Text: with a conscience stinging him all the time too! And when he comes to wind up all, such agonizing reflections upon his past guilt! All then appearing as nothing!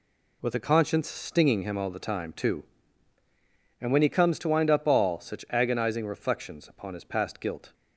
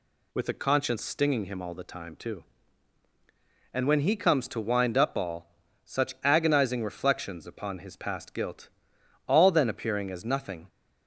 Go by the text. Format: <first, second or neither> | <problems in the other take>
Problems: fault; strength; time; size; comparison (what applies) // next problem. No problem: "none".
second | stops before "All then appearing as nothing"; at 7.7 s